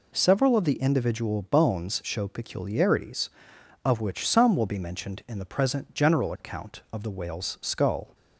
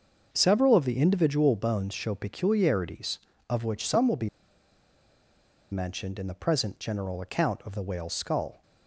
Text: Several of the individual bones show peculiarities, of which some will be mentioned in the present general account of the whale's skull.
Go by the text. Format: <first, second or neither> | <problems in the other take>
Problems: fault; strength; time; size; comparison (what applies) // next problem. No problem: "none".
first | starts louder than the rest; until 1.3 s; 6 dB // pauses between "be" and "mentioned"; strong; at 4.2 s; 1.4 s long